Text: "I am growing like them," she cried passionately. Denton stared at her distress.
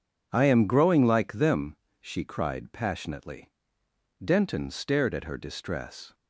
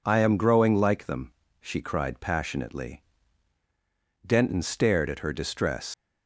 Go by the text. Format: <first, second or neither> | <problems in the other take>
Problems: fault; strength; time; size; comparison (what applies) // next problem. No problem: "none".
first | leaves "distress" unfinished; at 5.9 s; 95 ms